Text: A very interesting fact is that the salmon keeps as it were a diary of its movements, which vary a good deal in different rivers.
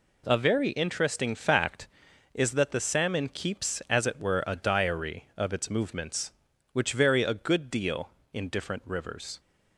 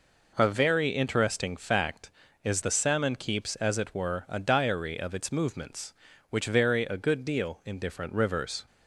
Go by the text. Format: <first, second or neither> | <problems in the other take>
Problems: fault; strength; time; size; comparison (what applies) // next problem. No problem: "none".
first | skips "that"; at 2.6 s